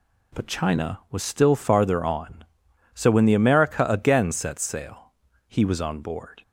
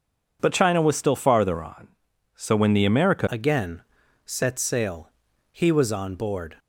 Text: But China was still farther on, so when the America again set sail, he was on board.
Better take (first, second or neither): first